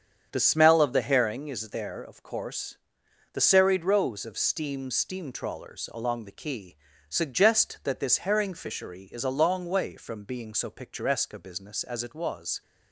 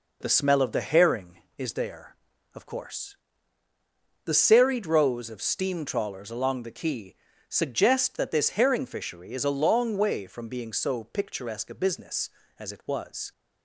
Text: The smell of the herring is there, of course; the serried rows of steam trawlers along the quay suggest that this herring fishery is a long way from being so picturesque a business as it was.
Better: second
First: starts louder than the rest; strong; until 1.3 s; 7.5 dB // says "steam" twice; at 4.8 s // pauses between "quay" and "suggest"; slight; at 6.7 s; 0.32 s long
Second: pauses between "quay" and "suggest"; slight; at 7.1 s; 0.34 s long

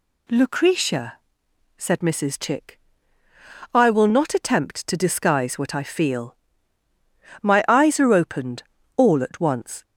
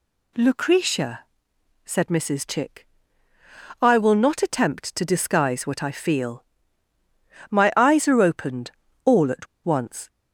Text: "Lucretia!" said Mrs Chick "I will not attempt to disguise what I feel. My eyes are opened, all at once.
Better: first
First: pauses between "Chick" and "I"; noticeable; at 2.7 s; 0.96 s long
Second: pauses between "Chick" and "I"; noticeable; at 2.8 s; 0.96 s long // pauses between "at" and "once"; slight; at 9.4 s; 0.18 s long

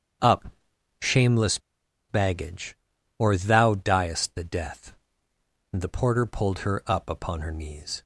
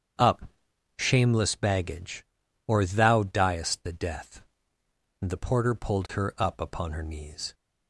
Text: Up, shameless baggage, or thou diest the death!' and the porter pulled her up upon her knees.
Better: second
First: starts louder than the rest; strong; until 2.2 s; 7.5 dB // pauses between "shameless" and "baggage"; noticeable; at 1.5 s; 0.51 s long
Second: starts louder than the rest; strong; until 1.6 s; 7.5 dB

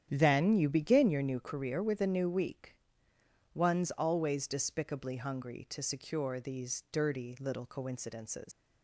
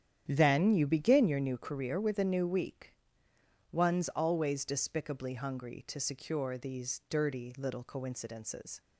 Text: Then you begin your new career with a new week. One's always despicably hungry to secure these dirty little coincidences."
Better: second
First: starts louder than the rest; strong; until 1.1 s; 9.5 dB // leaves "coincidences" unfinished; at 8.5 s; 115 ms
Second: starts louder than the rest; strong; until 1.2 s; 9.5 dB

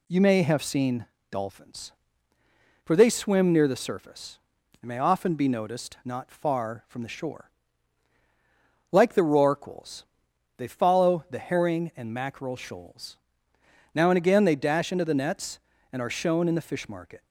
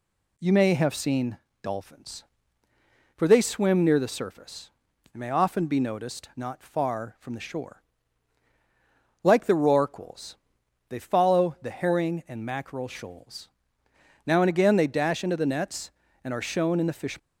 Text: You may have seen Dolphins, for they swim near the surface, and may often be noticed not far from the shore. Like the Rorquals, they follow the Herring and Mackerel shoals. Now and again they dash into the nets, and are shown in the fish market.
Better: first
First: pauses between "seen" and "Dolphins"; slight; at 1.0 s; 0.24 s long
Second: pauses between "seen" and "Dolphins"; slight; at 1.3 s; 0.24 s long // stops before "market"; at 17.1 s

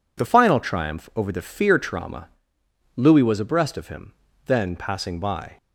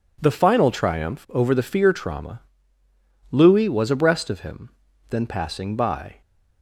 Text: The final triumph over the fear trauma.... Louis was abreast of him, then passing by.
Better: neither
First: none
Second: none

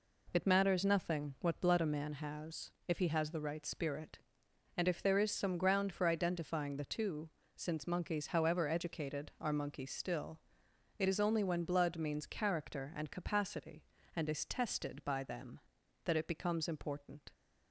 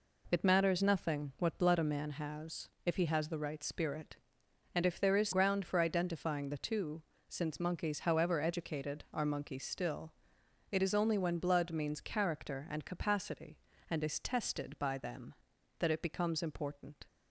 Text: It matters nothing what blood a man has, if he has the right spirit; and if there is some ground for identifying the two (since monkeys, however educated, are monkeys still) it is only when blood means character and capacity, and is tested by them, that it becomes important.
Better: first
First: none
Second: skips "some"; at 5.3 s

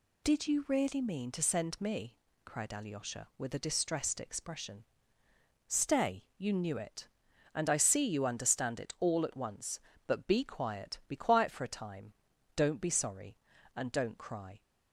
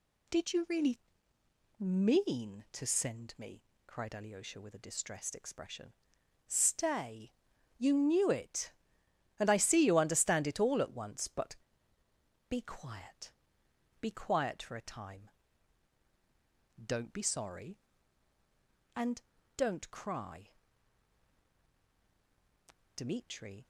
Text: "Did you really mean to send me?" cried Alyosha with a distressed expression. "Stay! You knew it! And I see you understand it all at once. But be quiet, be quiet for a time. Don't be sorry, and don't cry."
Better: first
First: none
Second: pauses between "really" and "mean"; noticeable; at 0.9 s; 0.80 s long // pauses between "But" and "be"; noticeable; at 11.5 s; 0.94 s long // pauses between "and" and "don't"; slight; at 19.2 s; 0.34 s long // goes on to say "Dmitri"; noticeable; from 22.9 s on; 0.72 s long

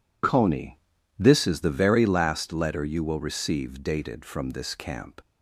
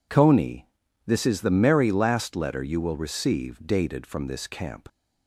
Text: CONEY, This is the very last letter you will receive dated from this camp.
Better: first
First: none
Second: says "merry" for "very"; at 1.4 s

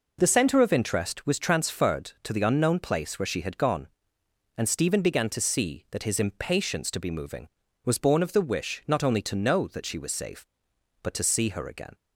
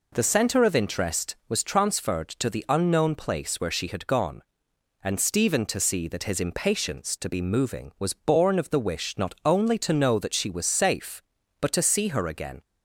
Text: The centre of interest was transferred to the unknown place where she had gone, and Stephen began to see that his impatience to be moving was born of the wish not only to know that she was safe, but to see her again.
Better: first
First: none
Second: skips "began"; at 5.6 s

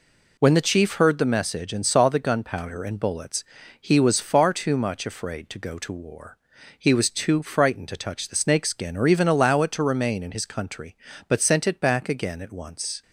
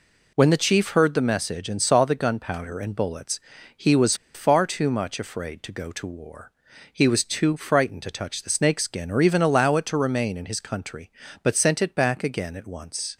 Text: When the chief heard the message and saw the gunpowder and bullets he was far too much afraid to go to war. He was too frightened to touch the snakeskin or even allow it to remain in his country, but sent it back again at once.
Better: first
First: pauses between "bullets" and "he"; at 3.4 s; 0.38 s long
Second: pauses between "bullets" and "he"; at 3.3 s; 0.38 s long // pauses between "was" and "far"; slight; at 4.1 s; 0.19 s long

